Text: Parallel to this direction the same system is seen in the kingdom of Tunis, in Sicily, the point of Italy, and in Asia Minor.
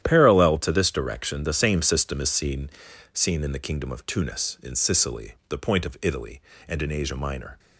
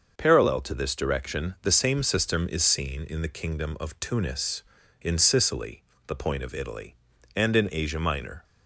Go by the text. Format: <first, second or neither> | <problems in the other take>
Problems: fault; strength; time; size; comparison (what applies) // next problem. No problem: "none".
second | starts louder than the rest; strong; until 1.0 s; 11 dB; also in the second // says "seen" twice; at 3.1 s